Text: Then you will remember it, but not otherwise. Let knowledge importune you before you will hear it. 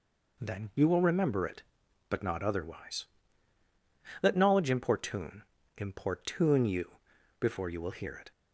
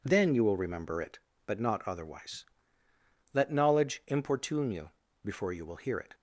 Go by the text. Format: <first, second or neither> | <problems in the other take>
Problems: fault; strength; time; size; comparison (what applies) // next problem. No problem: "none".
second | says "importune" twice; at 5.7 s // pauses between "you" and "before"; at 6.9 s; 0.42 s long; slight in the second